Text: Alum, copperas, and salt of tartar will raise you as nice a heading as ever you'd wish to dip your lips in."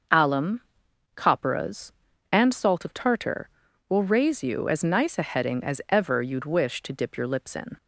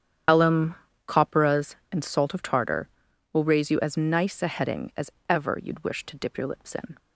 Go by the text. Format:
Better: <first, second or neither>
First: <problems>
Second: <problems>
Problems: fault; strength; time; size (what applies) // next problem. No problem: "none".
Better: first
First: starts louder than the rest; noticeable; until 1.6 s; 6 dB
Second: loses the start of "Alum"; at 0.2 s; 95 ms // starts louder than the rest; strong; until 1.5 s; 9.5 dB // pauses between "as" and "ever"; slight; at 5.0 s; 0.18 s long